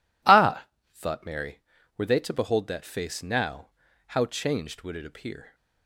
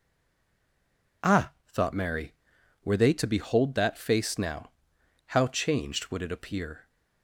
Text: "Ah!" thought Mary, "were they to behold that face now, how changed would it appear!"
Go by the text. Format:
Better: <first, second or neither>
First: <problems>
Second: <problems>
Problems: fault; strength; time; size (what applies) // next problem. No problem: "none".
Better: first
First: none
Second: stays silent before the first word; noticeable; until 1.2 s; 1.2 s long